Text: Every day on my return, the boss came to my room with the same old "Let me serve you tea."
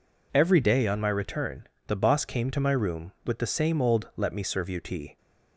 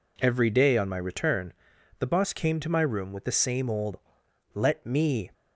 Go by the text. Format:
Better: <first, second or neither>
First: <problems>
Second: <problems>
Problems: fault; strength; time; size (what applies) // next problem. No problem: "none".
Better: first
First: none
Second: pauses between "old" and "Let"; noticeable; at 3.9 s; 0.56 s long // stops before "serve you tea"; at 5.3 s